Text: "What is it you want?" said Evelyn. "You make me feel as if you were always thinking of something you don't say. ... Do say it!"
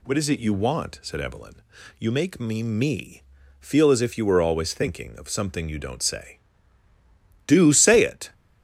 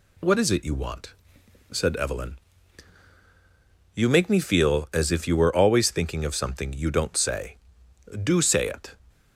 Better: second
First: says "me" twice; at 2.6 s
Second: none

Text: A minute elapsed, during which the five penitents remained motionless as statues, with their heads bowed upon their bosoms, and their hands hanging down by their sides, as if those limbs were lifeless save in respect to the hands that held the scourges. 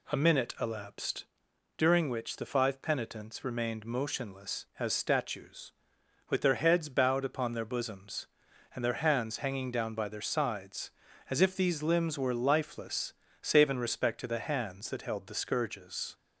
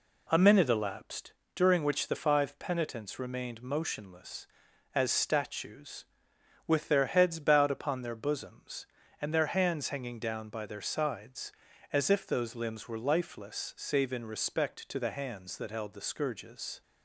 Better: second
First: says "these" for "those"; at 11.5 s // pauses between "lifeless" and "save"; slight; at 13.1 s; 0.28 s long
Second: none

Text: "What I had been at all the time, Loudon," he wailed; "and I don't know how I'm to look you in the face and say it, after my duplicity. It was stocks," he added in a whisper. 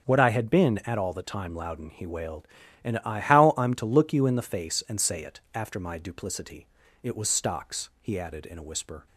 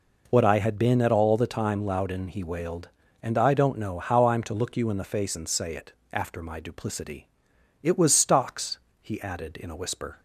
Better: second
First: starts louder than the rest; strong; until 1.0 s; 7 dB // skips "don't know"; at 3.1 s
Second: none

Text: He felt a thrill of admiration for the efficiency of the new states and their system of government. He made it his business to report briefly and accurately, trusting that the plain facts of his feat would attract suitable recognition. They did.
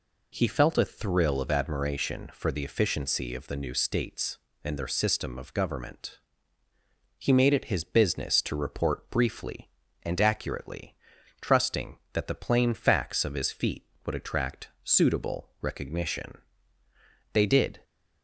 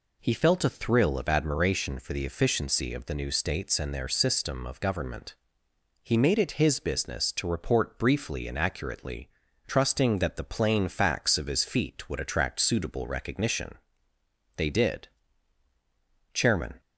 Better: first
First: none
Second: goes on to say "Chairman"; slight; from 16.3 s on; 0.46 s long

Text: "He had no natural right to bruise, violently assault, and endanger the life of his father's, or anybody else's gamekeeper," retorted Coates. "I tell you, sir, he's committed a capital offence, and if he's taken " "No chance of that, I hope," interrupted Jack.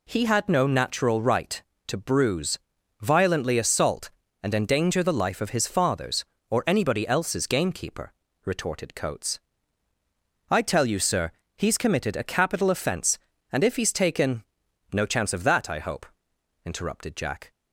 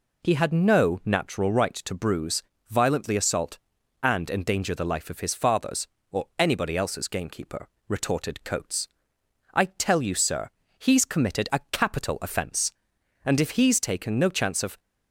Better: first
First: none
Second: stops before "that I hope interrupted Jack"; at 14.7 s

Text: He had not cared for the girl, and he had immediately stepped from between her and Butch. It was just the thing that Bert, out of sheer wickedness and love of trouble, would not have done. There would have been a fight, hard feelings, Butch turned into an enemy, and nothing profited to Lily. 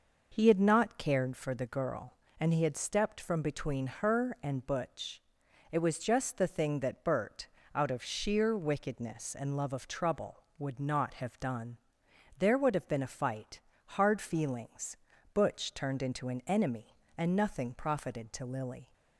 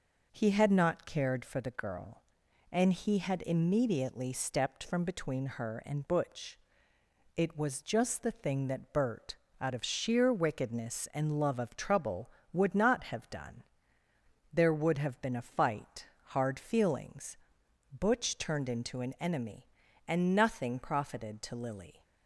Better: second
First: skips "immediately"; at 2.7 s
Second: none

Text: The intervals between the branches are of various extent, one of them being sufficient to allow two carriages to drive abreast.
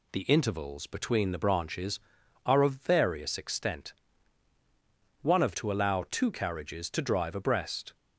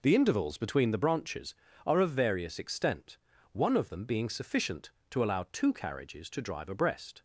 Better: second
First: skips "them being sufficient"; at 5.5 s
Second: none

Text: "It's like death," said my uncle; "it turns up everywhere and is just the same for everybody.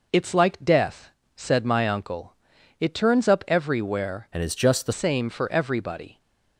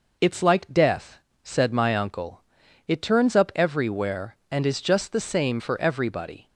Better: second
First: changes voice from "and" to "the"; from 4.3 to 4.9 s; 0.6 s long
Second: none

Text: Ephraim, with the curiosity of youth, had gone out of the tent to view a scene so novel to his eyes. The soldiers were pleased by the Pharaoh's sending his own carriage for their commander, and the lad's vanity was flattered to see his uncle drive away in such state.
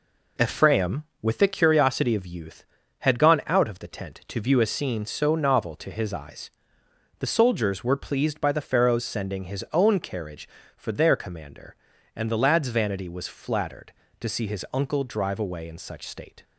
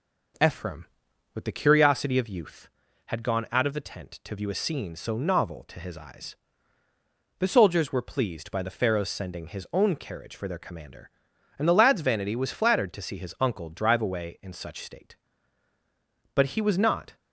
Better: first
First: none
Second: goes on to say "But he was not"; noticeable; from 16.3 s on; 0.82 s long

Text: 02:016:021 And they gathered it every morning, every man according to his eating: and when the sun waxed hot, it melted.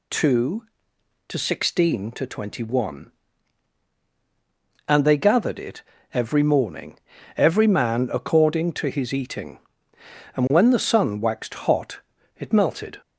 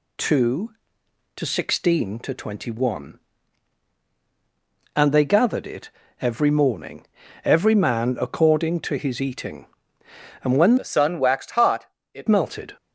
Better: first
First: pauses between "it" and "every"; slight; at 5.8 s; 0.30 s long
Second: pauses between "it" and "every"; slight; at 5.8 s; 0.30 s long // changes voice from "the" to "it"; from 10.7 to 12.2 s; 1.5 s long

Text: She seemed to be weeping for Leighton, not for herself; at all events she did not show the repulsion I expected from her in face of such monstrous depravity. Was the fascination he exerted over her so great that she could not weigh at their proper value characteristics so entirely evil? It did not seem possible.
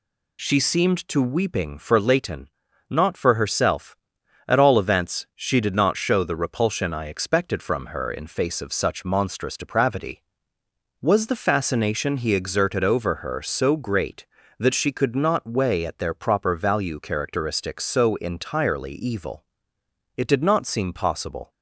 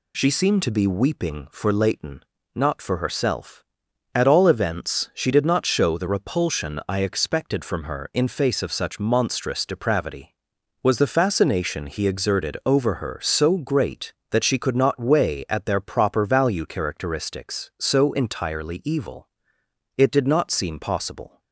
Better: second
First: skips "be"; at 1.1 s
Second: none

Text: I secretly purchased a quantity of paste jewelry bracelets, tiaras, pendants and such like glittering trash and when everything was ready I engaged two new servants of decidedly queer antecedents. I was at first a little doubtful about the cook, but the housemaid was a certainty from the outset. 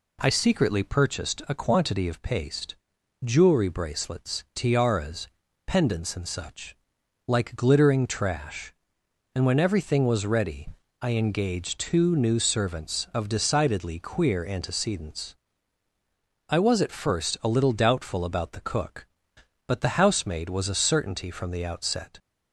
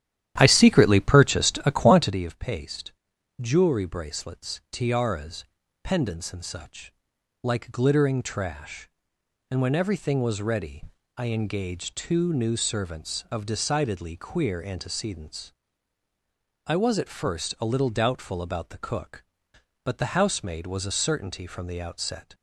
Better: first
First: pauses between "paste" and "jewelry"; noticeable; at 2.7 s; 0.48 s long // pauses between "such" and "like"; noticeable; at 6.7 s; 0.50 s long // pauses between "ready" and "I"; slight; at 10.6 s; 0.32 s long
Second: starts louder than the rest; strong; until 2.2 s; 11.5 dB // pauses between "paste" and "jewelry"; noticeable; at 2.9 s; 0.48 s long // pauses between "such" and "like"; noticeable; at 6.9 s; 0.48 s long // pauses between "ready" and "I"; slight; at 10.8 s; 0.32 s long

